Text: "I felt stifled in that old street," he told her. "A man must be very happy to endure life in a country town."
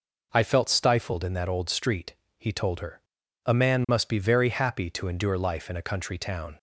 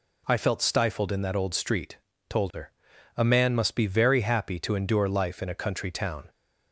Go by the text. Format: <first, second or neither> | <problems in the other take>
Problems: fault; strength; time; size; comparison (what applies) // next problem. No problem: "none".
first | skips "he"; at 2.1 s